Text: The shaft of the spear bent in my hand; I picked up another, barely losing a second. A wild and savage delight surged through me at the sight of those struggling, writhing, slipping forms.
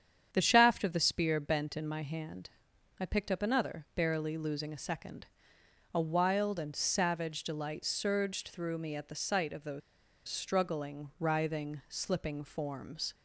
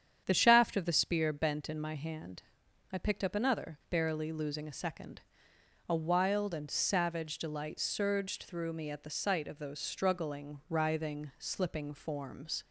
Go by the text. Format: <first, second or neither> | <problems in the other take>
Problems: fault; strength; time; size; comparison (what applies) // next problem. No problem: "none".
second | starts louder than the rest; strong; until 1.3 s; 8.5 dB; strong in the second // pauses between "those" and "struggling"; noticeable; at 9.8 s; 0.47 s long